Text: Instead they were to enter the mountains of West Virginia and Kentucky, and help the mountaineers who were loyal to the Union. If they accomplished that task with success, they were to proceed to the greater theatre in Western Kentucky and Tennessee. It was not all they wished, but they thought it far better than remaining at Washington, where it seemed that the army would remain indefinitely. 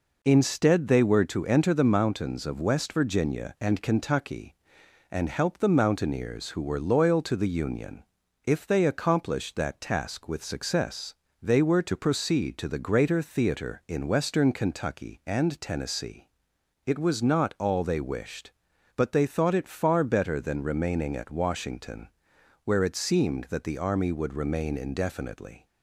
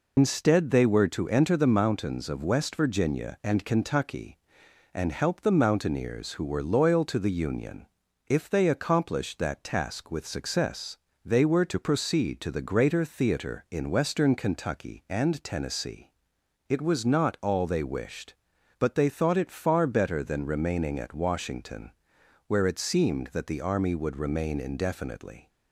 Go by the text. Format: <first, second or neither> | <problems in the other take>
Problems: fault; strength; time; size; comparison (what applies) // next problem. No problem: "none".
first | loses the start of "Instead"; at 0.1 s; 105 ms